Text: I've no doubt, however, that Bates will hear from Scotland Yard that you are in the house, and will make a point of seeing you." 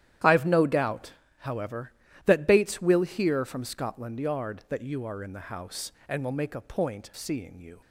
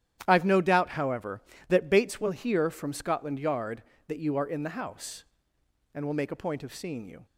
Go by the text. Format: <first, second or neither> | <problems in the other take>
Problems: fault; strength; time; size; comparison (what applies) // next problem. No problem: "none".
second | starts louder than the rest; strong; until 1.5 s; 11.5 dB; strong in the second // skips "of"; at 7.1 s